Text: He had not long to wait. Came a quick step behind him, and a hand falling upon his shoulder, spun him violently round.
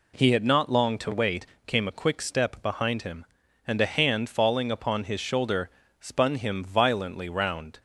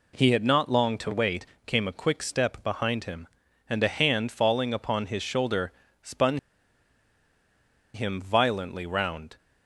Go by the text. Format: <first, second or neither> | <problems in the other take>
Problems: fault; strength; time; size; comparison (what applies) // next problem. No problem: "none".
first | pauses between "spun" and "him"; strong; at 6.3 s; 1.5 s long